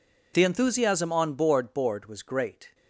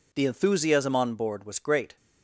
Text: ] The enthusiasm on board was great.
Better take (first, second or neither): second